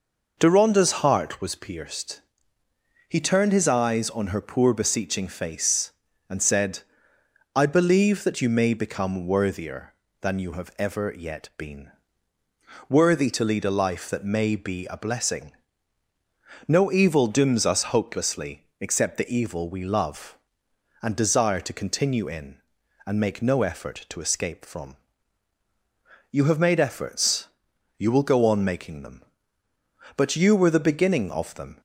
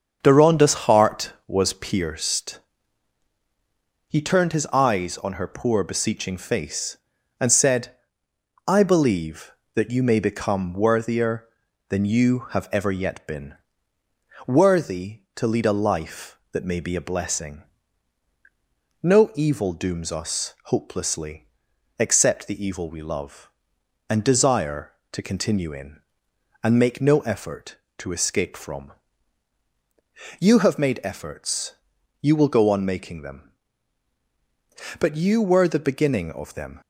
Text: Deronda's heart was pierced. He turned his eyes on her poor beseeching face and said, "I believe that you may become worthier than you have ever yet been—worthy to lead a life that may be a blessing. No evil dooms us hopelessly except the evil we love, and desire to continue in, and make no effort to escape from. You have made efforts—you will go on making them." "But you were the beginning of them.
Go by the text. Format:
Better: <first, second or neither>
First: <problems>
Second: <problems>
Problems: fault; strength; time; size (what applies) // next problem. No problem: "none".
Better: first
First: none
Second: starts louder than the rest; strong; until 2.1 s; 7 dB // pauses between "hopelessly" and "except"; noticeable; at 21.4 s; 0.50 s long